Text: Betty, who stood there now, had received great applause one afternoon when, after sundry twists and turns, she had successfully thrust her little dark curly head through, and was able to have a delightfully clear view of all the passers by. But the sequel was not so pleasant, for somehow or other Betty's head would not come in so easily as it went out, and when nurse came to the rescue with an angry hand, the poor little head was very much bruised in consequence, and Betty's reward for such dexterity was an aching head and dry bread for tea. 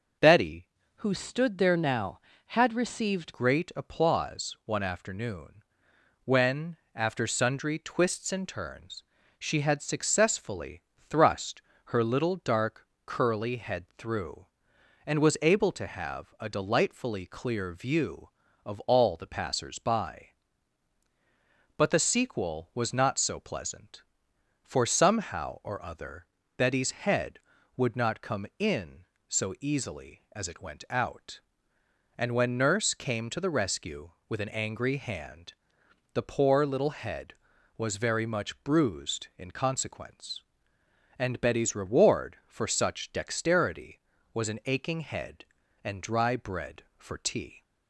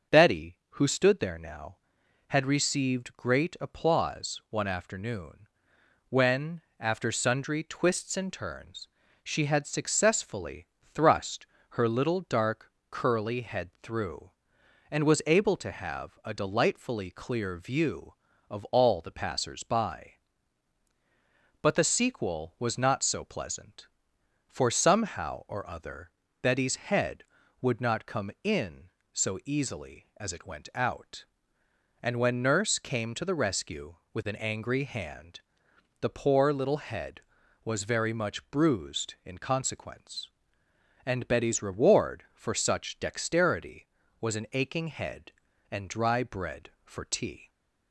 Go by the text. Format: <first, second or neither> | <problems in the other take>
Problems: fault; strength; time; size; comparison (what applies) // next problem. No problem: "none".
second | starts louder than the rest; until 1.5 s; 6.5 dB; also in the second // changes voice from "who" to "received"; from 0.9 to 3.3 s; 2.4 s long // pauses between "afternoon" and "when"; noticeable; at 5.6 s; 0.64 s long; noticeable in the second // pauses between "successfully" and "thrust"; slight; at 10.7 s; 0.30 s long; slight in the second // pauses between "thrust" and "her"; slight; at 11.5 s; 0.26 s long; slight in the second // pauses between "dark" and "curly"; slight; at 12.8 s; 0.18 s long; slight in the second // pauses between "other" and "Betty's"; slight; at 26.2 s; 0.32 s long; slight in the second